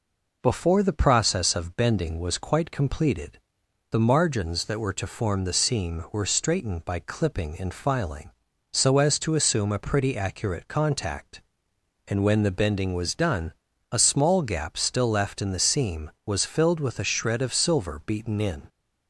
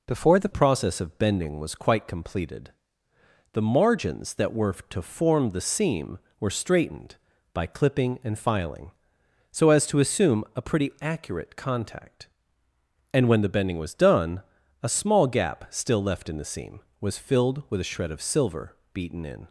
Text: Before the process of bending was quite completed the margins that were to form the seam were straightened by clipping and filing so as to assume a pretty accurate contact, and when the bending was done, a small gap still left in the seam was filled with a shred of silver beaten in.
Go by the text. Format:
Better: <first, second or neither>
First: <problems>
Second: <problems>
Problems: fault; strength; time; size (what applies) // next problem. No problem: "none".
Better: first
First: pauses between "completed" and "the"; noticeable; at 3.3 s; 0.52 s long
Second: changes voice at "process"; from 0.5 s on; 18.9 s long // pauses between "completed" and "the"; noticeable; at 2.7 s; 0.80 s long // pauses between "silver" and "beaten"; slight; at 18.7 s; 0.16 s long